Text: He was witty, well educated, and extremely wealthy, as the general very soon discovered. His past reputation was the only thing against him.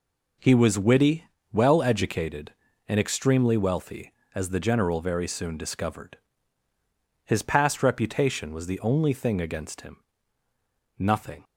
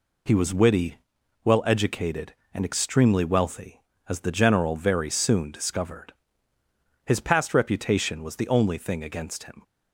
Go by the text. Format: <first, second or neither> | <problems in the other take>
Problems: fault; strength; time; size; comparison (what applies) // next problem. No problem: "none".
second | goes on to say "Nothing"; slight; from 10.9 s on; 0.46 s long